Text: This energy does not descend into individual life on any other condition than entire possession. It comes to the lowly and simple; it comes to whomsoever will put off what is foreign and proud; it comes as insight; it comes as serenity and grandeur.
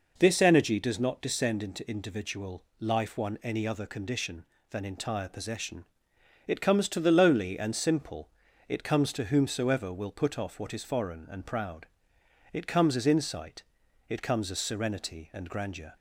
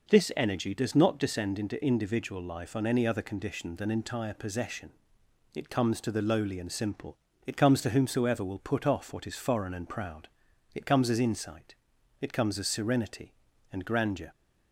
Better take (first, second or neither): second